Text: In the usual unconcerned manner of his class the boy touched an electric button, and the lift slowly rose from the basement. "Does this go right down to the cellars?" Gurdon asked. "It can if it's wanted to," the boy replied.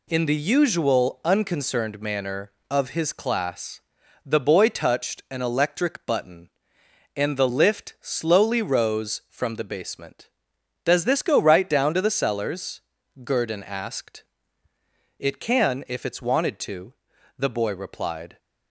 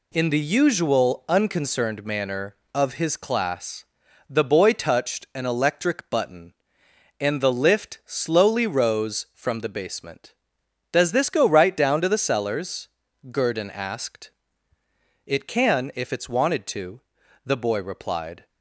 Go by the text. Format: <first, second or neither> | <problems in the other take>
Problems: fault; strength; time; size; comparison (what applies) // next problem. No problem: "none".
neither | pauses between "class" and "the"; the same in both